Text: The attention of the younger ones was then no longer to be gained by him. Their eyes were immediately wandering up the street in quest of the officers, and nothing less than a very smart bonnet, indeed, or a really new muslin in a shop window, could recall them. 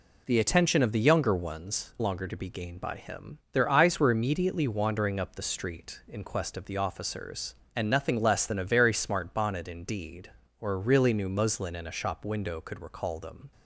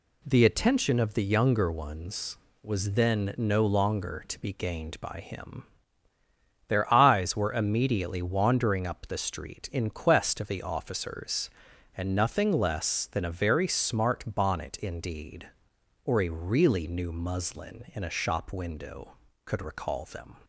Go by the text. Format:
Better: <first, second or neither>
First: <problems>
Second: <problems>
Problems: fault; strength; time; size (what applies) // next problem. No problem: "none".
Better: second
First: skips "was then no"; at 1.9 s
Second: none